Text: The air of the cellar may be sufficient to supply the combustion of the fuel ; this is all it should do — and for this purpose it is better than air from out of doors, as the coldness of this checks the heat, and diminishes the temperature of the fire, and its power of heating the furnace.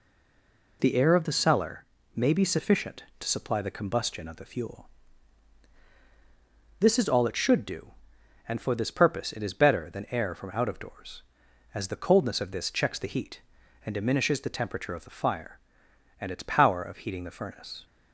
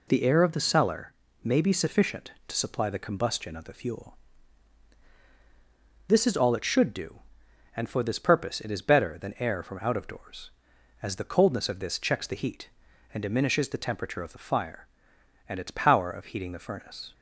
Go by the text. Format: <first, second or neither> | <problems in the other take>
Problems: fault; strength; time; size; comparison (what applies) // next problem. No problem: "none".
second | stays silent before the first word; slight; until 0.8 s; 0.8 s long // pauses between "cellar" and "may"; slight; at 1.8 s; 0.30 s long; slight in the second